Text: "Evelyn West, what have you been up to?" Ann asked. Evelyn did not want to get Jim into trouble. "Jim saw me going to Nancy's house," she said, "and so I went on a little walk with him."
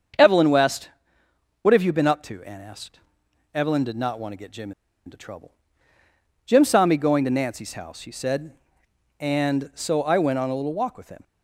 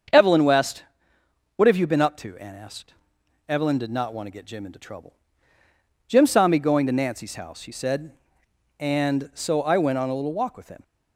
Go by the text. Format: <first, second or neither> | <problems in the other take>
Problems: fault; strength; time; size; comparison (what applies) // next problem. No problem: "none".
second | starts louder than the rest; strong; until 1.9 s; 7 dB; strong in the second // pauses between "Jim" and "into"; slight; at 4.7 s; 0.35 s long